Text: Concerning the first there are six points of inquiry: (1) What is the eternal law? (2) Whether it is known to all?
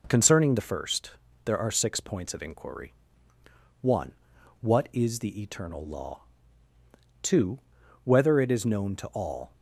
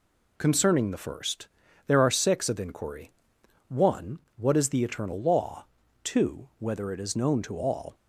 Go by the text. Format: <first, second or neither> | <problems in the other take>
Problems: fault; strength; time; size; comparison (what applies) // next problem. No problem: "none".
first | pauses between "first" and "there"; at 1.4 s; 0.40 s long; slight in the first // skips "points"; at 2.4 s